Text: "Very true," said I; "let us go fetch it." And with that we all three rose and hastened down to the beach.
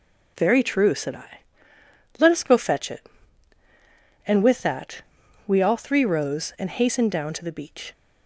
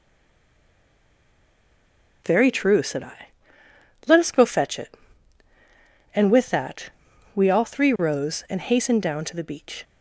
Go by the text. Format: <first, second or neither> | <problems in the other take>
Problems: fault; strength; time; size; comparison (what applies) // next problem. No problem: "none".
first | stays silent before the first word; until 2.2 s; 2.2 s long // pauses between "that" and "we"; at 6.9 s; 0.44 s long; also in the first